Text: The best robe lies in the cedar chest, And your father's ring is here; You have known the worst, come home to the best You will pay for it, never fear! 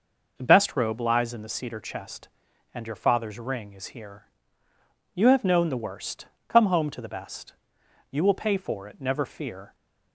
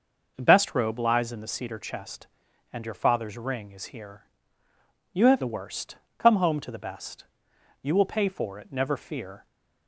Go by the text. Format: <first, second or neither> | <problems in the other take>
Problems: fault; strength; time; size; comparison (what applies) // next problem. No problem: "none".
first | skips "known"; at 5.4 s // pauses between "best" and "You"; noticeable; at 7.2 s; 0.58 s long; noticeable in the first